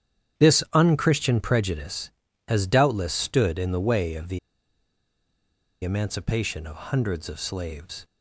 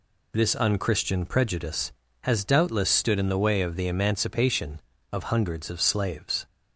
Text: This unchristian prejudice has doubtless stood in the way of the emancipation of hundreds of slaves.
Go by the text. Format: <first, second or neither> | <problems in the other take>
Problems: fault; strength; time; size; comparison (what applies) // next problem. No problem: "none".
second | starts louder than the rest; strong; until 1.5 s; 10 dB // pauses between "the" and "emancipation"; strong; at 4.3 s; 1.4 s long